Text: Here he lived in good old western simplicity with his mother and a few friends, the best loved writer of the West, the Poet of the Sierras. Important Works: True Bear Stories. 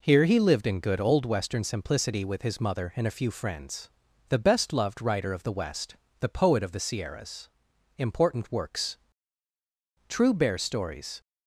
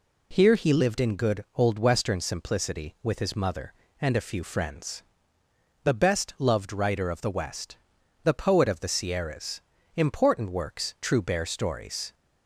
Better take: neither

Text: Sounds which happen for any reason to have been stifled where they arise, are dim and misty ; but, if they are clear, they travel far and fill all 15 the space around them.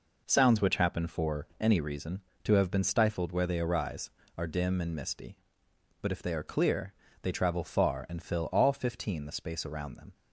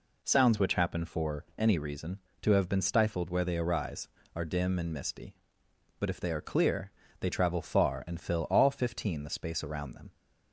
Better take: second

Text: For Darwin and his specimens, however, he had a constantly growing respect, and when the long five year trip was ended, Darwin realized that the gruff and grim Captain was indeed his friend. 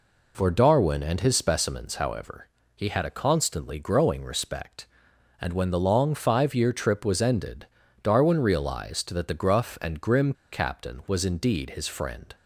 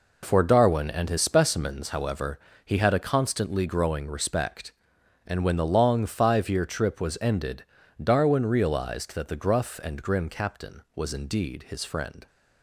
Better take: second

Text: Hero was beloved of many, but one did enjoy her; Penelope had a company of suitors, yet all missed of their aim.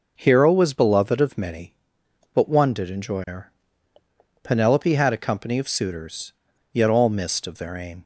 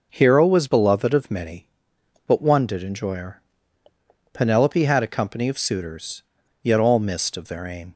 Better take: neither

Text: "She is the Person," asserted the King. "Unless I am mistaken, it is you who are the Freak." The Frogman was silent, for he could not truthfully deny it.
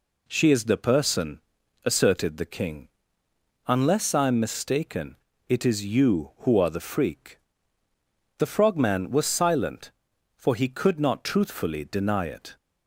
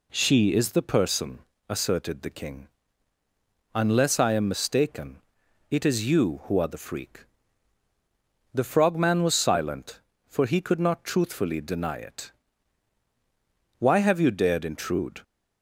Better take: first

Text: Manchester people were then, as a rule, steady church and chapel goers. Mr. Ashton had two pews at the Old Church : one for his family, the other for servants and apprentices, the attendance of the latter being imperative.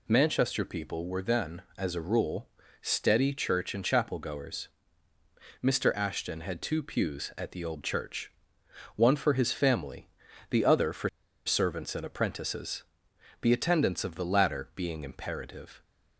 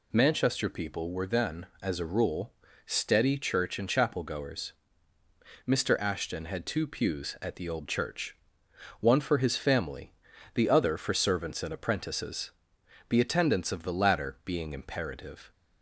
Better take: second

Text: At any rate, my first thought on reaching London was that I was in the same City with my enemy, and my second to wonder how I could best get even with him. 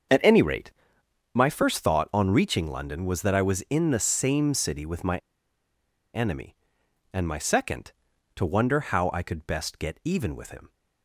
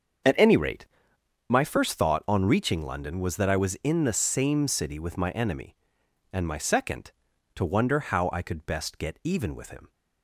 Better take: second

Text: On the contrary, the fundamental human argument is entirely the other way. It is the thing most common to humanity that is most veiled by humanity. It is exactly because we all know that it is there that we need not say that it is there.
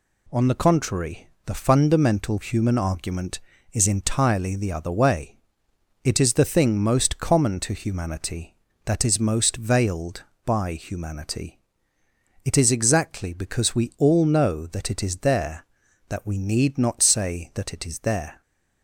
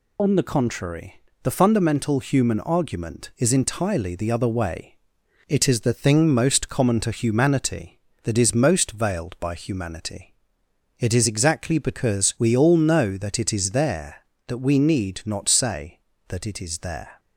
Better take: first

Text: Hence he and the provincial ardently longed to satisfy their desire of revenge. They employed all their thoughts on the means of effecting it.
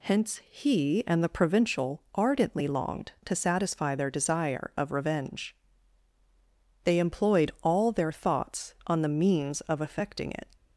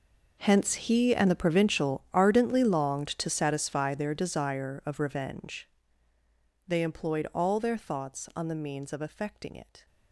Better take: first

